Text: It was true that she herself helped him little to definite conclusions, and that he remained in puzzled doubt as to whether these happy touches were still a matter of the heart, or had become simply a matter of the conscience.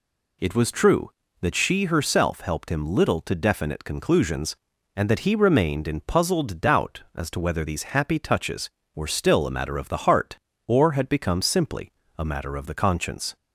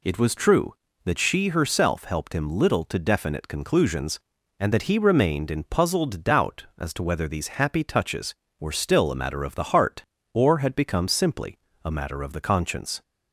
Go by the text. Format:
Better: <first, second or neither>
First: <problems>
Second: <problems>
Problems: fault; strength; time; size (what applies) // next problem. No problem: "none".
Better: neither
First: pauses between "simply" and "a"; slight; at 11.9 s; 0.26 s long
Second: pauses between "simply" and "a"; slight; at 11.5 s; 0.26 s long